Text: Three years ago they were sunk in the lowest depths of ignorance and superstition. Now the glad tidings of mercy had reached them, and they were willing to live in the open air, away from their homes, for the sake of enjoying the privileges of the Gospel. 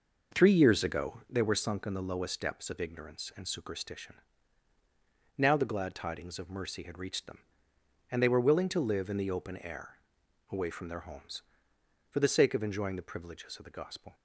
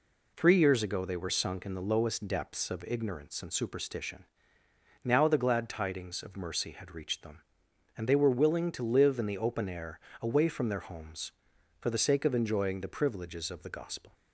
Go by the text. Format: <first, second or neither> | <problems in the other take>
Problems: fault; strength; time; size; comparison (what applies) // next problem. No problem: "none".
second | starts louder than the rest; noticeable; until 1.5 s; 5.5 dB